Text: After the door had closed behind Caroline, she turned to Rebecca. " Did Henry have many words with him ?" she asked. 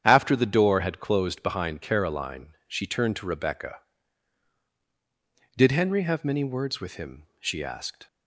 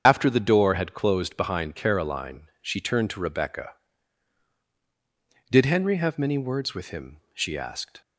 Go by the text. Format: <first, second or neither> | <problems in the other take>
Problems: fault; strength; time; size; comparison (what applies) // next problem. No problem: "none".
first | loses the start of "After"; at 0.0 s; 65 ms // starts louder than the rest; strong; until 1.0 s; 8.5 dB; strong in the first